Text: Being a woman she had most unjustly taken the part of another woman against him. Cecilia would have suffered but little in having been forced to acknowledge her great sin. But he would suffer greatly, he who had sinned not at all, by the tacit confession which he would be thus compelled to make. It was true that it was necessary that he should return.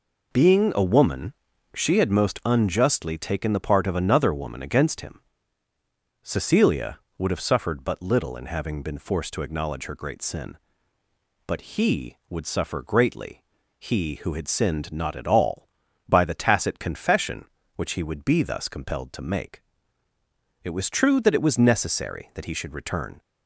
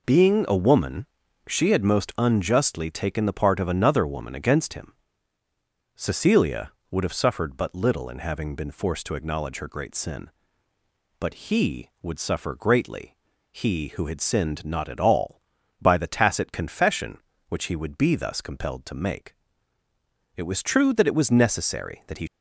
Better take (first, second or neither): first